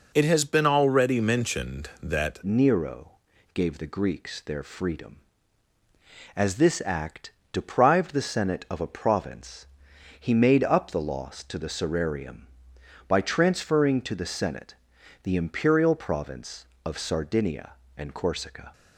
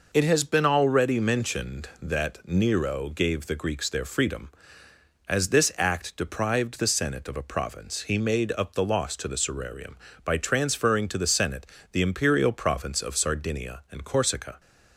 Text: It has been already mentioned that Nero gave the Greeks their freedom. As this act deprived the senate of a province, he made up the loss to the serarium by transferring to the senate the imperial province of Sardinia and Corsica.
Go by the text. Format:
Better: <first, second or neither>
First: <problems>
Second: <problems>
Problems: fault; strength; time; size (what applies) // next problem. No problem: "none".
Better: second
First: changes voice at "Nero"; from 2.4 s on; 16.3 s long // pauses between "Nero" and "gave"; at 3.1 s; 0.42 s long // pauses between "act" and "deprived"; slight; at 7.3 s; 0.22 s long // pauses between "senate" and "the"; noticeable; at 14.7 s; 0.48 s long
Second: pauses between "senate" and "the"; slight; at 11.6 s; 0.24 s long